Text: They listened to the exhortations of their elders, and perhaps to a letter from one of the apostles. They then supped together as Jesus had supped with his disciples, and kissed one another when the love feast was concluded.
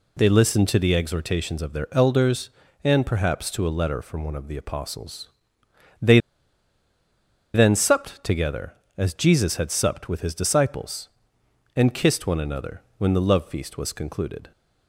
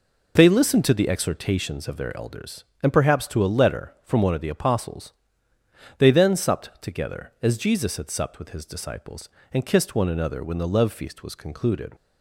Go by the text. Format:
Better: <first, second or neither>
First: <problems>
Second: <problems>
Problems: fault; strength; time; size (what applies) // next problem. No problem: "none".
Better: second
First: pauses between "They" and "then"; strong; at 6.1 s; 1.3 s long // pauses between "another" and "when"; slight; at 12.8 s; 0.18 s long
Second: none